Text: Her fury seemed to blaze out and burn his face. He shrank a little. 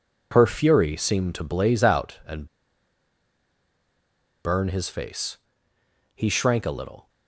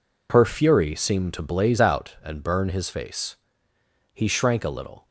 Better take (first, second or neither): second